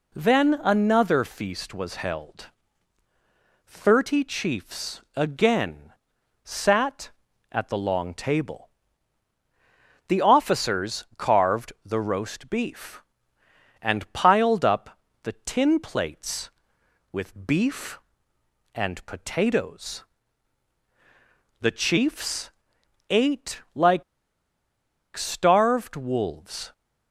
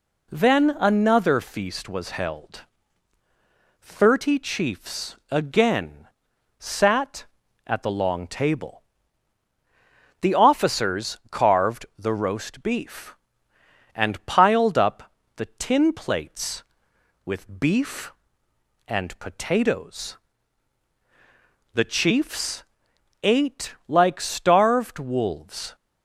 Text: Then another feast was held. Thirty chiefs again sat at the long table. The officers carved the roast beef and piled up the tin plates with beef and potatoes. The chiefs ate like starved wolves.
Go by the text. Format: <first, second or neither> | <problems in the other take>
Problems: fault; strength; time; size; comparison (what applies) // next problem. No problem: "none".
second | pauses between "chiefs" and "again"; slight; at 5.0 s; 0.16 s long; slight in the second // pauses between "again" and "sat"; noticeable; at 5.9 s; 0.52 s long; noticeable in the second // pauses between "up" and "the"; slight; at 14.9 s; 0.24 s long; slight in the second // pauses between "chiefs" and "ate"; noticeable; at 22.5 s; 0.58 s long; noticeable in the second // pauses between "like" and "starved"; at 24.0 s; 1.1 s long